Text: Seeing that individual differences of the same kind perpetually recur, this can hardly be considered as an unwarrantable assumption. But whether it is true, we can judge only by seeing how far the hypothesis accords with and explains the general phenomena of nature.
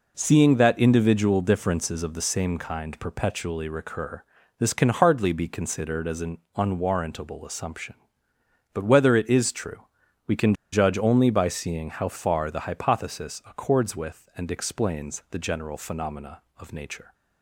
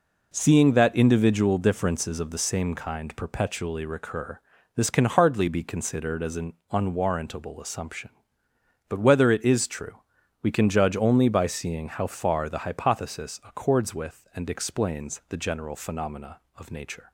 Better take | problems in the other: second | pauses between "an" and "unwarrantable"; slight; at 6.3 s; 0.18 s long; slight in the second // pauses between "can" and "judge"; slight; at 10.5 s; 0.18 s long

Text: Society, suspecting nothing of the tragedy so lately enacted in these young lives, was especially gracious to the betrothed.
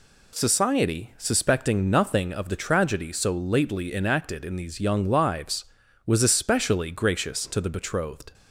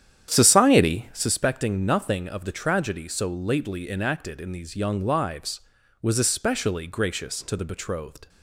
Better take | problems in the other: first | starts louder than the rest; strong; until 1.3 s; 10 dB

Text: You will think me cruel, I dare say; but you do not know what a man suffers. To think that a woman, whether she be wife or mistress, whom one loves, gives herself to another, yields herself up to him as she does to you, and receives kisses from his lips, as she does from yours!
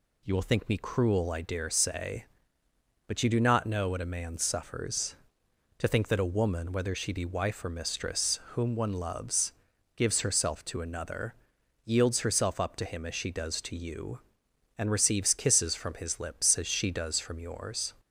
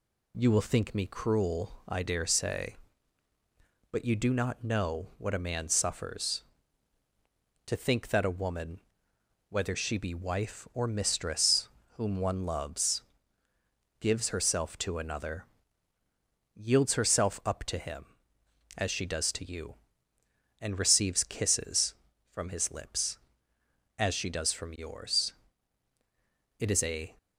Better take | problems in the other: first | goes on to say "It is a"; from 26.5 s on; 0.58 s long

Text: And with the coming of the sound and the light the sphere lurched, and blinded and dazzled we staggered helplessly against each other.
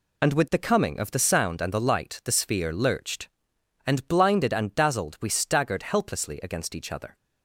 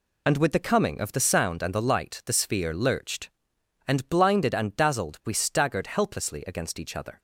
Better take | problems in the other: neither | none

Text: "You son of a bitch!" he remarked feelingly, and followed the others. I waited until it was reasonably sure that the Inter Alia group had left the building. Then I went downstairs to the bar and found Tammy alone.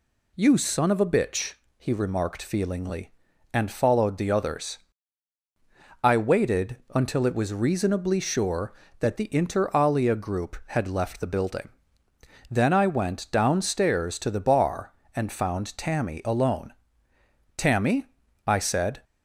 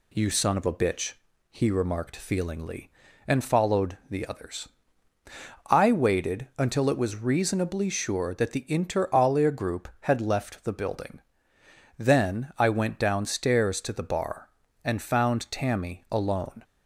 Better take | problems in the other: second | pauses between "waited" and "until"; slight; at 6.7 s; 0.18 s long // goes on to say "Tammy I said"; from 17.5 s on; 1.4 s long

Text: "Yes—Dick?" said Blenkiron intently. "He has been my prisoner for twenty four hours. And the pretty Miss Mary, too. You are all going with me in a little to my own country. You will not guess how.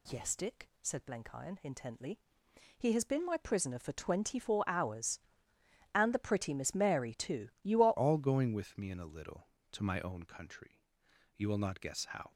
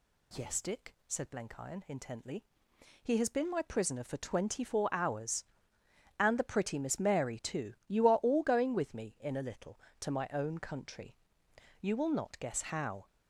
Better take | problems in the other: second | changes voice at "all"; from 7.9 s on; 4.4 s long

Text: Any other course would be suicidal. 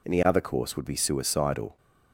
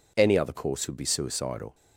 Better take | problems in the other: neither | none

